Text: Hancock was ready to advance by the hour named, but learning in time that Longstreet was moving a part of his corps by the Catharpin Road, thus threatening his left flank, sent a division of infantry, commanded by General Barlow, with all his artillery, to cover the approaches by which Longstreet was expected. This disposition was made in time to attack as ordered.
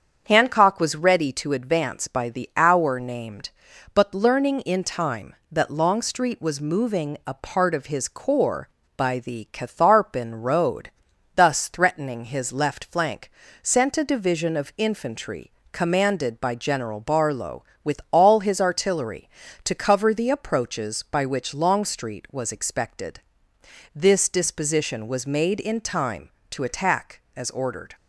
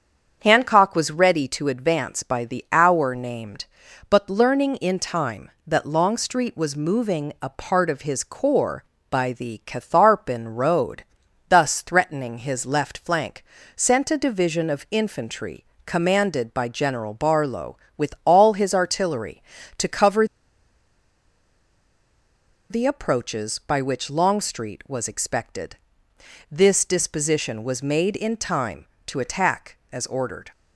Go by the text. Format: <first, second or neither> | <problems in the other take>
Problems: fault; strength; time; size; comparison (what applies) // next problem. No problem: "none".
first | starts louder than the rest; strong; until 1.4 s; 7.5 dB; strong in the first // pauses between "cover" and "the"; strong; at 20.2 s; 2.4 s long